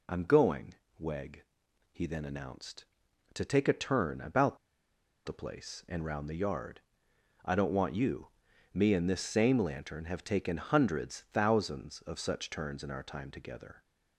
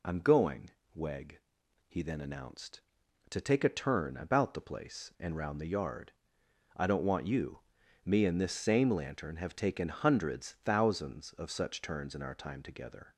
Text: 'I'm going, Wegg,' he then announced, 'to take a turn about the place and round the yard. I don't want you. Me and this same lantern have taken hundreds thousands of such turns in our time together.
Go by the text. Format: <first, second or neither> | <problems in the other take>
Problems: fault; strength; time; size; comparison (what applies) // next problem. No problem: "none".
second | pauses between "about" and "the"; noticeable; at 4.5 s; 0.68 s long